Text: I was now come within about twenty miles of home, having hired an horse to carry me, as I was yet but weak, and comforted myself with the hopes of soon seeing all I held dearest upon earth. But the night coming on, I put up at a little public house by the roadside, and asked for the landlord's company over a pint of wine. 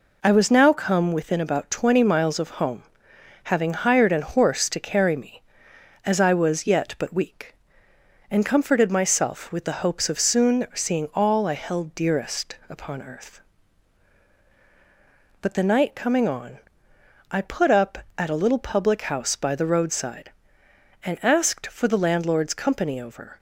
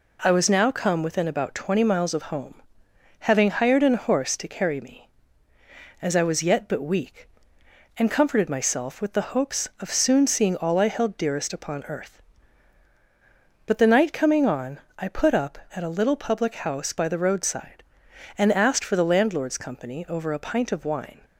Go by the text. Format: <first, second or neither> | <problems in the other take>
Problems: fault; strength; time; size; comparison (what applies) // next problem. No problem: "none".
second | stops before "a pint of wine"; at 23.3 s